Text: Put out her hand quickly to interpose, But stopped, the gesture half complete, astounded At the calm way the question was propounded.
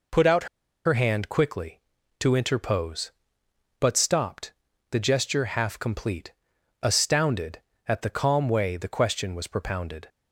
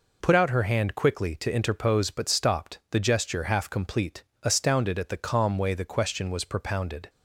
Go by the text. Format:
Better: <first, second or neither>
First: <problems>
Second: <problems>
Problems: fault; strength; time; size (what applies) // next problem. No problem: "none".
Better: second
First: pauses between "out" and "her"; at 0.4 s; 0.40 s long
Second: none